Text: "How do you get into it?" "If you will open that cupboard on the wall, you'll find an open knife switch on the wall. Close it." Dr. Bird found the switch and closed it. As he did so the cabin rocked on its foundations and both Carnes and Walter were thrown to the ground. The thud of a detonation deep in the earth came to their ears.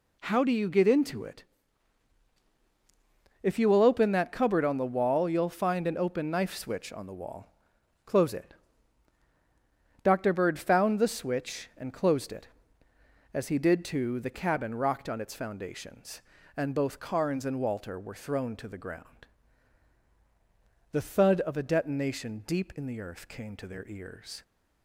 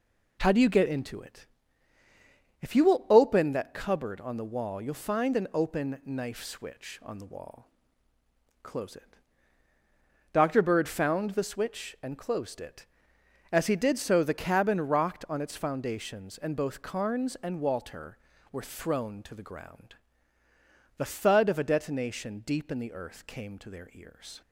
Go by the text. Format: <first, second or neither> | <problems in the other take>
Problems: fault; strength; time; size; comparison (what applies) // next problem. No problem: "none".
second | says "too" for "so"; at 13.8 s